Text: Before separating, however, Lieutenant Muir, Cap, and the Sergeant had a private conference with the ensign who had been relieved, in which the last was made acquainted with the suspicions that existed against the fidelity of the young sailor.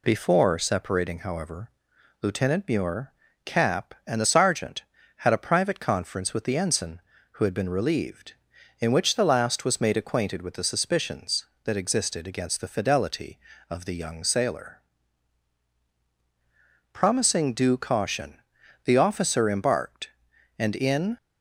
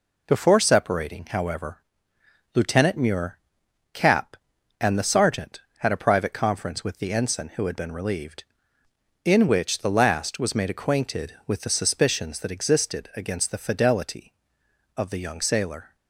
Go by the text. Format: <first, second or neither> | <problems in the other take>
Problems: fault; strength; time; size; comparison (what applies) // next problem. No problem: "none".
second | goes on to say "Promising due caution the officer embarked and in"; strong; from 16.9 s on; 4.2 s long